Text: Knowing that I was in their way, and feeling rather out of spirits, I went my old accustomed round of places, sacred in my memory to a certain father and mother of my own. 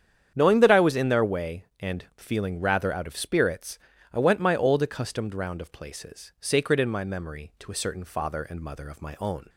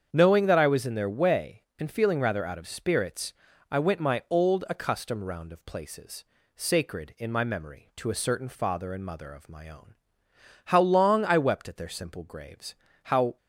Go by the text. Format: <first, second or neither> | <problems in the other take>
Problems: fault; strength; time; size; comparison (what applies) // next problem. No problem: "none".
first | starts louder than the rest; strong; until 1.1 s; 7.5 dB; strong in the first // goes on to say "How long I wept at their simple graves how"; strong; from 10.6 s on; 2.7 s long